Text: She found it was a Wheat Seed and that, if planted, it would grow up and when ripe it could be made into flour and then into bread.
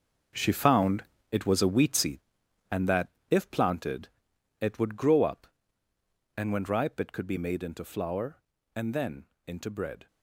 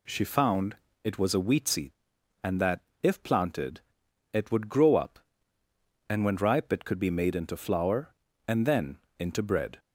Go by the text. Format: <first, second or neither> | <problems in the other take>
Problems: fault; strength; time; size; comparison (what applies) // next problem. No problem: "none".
second | gets quieter; strong; throughout; 12 dB // pauses between "found" and "it"; slight; at 1.0 s; 0.26 s long; slight in the second // pauses between "then" and "into"; slight; at 9.2 s; 0.18 s long; slight in the second